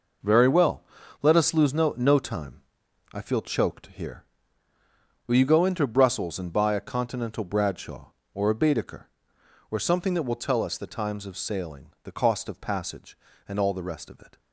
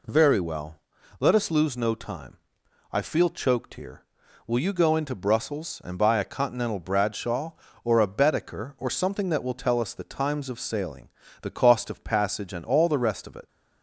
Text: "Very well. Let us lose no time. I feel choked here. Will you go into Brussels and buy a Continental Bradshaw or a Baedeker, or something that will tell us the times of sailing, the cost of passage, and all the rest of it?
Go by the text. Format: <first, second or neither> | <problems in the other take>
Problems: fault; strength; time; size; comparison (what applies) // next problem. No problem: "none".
second | says "no" twice; at 1.9 s